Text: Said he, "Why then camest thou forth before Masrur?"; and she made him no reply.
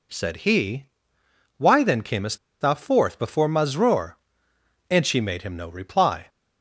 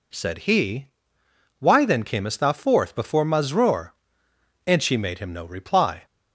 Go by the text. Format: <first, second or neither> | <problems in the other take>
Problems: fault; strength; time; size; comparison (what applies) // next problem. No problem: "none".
second | pauses between "camest" and "thou"; slight; at 2.3 s; 0.24 s long